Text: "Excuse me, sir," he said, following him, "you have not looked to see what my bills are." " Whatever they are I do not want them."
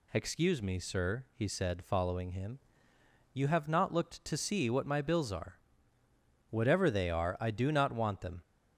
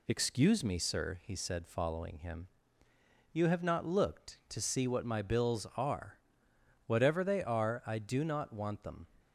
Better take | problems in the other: neither | none

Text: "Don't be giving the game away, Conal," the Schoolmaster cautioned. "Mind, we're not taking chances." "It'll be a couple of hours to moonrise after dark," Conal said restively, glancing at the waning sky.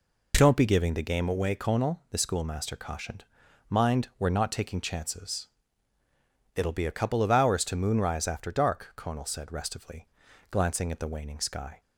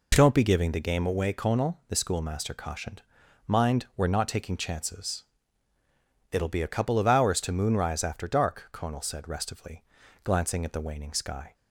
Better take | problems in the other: neither | none

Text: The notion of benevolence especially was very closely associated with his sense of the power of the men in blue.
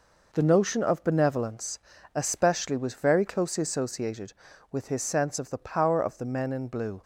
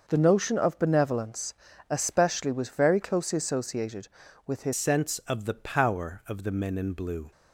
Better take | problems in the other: first | pauses between "benevolence" and "especially"; slight; at 1.5 s; 0.34 s long; slight in the first // changes voice at "sense"; from 4.7 s on; 2.6 s long

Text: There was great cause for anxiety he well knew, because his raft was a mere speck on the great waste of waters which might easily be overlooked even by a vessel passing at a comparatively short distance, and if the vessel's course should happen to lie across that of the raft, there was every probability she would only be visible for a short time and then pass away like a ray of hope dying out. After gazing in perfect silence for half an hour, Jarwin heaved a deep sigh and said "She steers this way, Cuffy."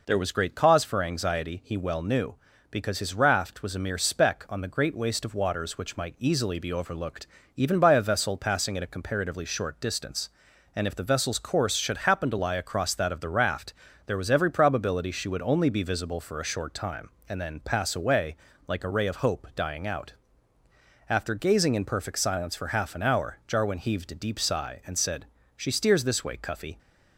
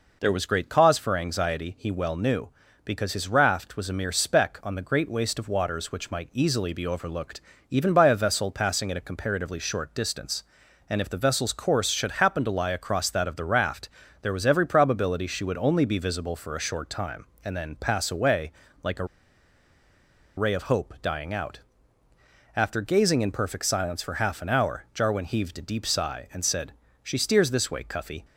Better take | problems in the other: first | pauses between "overlooked" and "even"; slight; at 7.4 s; 0.28 s long; slight in the first // pauses between "away" and "like"; slight; at 18.5 s; 0.30 s long; slight in the first // pauses between "a" and "ray"; strong; at 19.0 s; 1.3 s long // pauses between "said" and "She"; slight; at 26.7 s; 0.30 s long; slight in the first

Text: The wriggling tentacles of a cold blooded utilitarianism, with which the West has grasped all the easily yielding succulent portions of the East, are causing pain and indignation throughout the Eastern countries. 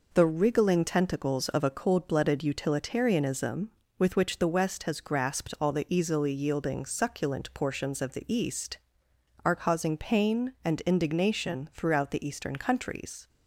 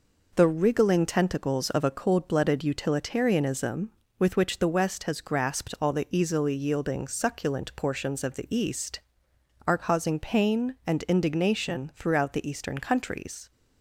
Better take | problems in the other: neither | none

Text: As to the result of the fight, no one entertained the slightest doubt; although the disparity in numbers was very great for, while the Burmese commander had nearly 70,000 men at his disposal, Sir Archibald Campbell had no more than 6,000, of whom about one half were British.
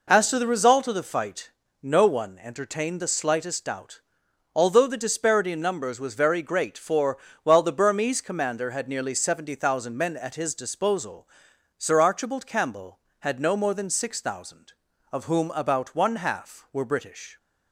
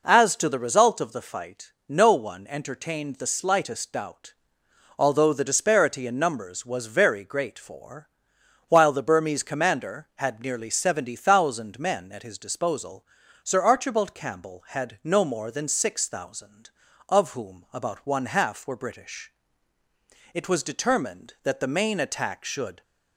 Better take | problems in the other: first | goes on to say "It was determined that the main attack should"; strong; from 20.3 s on; 2.4 s long

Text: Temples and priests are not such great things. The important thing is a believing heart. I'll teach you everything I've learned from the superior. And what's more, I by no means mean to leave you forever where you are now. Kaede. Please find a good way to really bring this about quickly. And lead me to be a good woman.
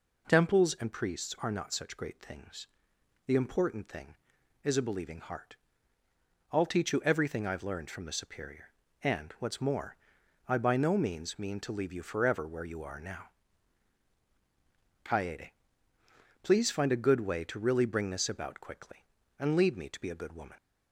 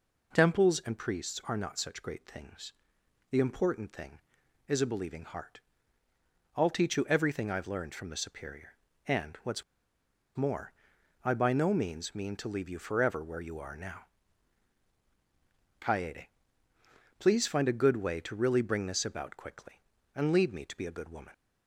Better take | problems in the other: first | pauses between "what's" and "more"; noticeable; at 9.6 s; 0.73 s long

